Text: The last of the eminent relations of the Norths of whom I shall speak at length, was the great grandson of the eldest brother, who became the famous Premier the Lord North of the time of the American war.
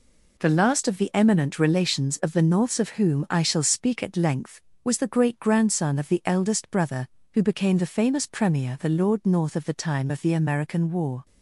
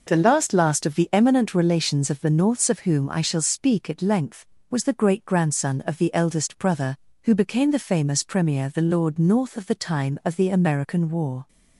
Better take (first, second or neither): first